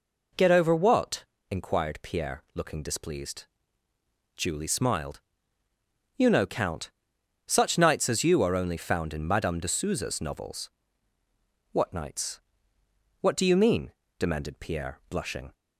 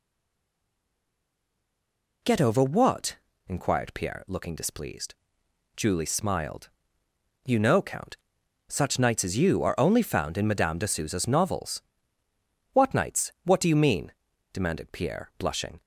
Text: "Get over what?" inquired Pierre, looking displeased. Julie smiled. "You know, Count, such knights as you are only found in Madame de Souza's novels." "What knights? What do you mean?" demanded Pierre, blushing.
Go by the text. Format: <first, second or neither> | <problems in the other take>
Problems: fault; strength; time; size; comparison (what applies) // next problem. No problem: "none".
first | stays silent before the first word; until 2.2 s; 2.2 s long